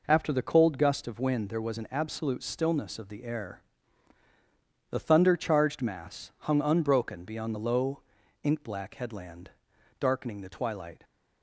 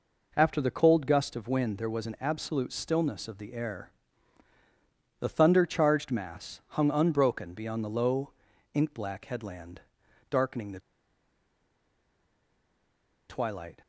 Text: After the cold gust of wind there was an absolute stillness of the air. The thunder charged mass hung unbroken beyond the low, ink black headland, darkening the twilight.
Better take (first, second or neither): first